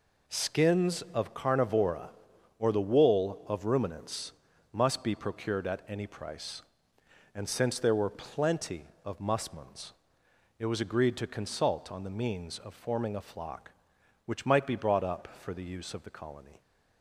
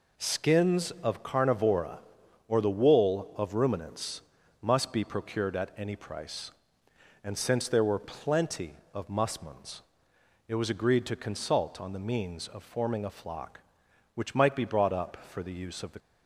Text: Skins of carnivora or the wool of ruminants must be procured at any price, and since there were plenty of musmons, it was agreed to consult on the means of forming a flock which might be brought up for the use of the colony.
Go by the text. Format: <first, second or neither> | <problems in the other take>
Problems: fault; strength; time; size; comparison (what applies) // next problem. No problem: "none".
first | pauses between "ruminants" and "must"; at 4.2 s; 0.40 s long; also in the first // stops before "colony"; at 15.9 s